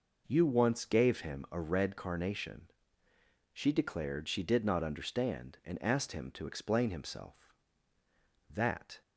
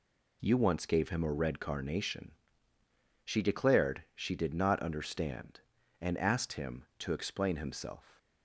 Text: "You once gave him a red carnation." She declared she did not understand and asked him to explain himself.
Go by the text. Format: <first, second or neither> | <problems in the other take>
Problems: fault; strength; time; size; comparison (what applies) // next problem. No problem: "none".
second | goes on to say "That"; from 8.4 s on; 0.52 s long